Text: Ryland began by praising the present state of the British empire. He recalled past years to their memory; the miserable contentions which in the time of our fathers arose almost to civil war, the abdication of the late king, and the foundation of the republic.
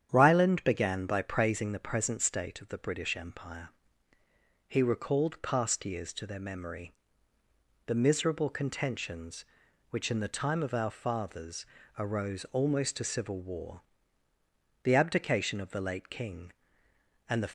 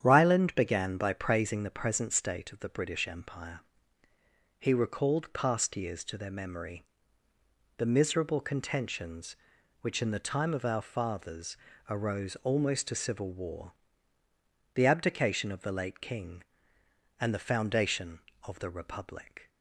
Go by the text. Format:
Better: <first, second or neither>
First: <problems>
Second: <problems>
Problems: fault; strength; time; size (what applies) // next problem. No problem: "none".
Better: second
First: starts louder than the rest; strong; until 1.1 s; 9 dB // pauses between "fathers" and "arose"; slight; at 11.6 s; 0.28 s long // stops before "foundation of the republic"; at 17.4 s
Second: starts louder than the rest; strong; until 1.0 s; 9 dB // pauses between "fathers" and "arose"; slight; at 11.5 s; 0.28 s long